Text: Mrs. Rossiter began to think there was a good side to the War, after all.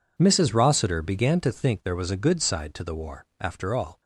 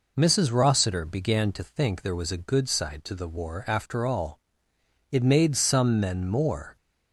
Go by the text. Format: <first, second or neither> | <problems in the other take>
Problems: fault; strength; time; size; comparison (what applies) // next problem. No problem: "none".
first | goes on to say "It made some men more"; from 5.1 s on; 1.6 s long